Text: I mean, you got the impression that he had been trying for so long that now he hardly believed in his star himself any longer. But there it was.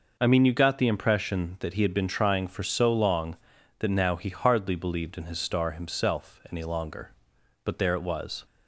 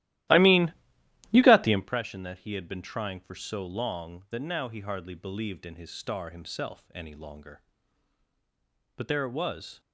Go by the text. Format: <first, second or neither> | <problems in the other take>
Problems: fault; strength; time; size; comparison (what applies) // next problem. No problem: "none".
first | starts louder than the rest; strong; until 2.0 s; 15 dB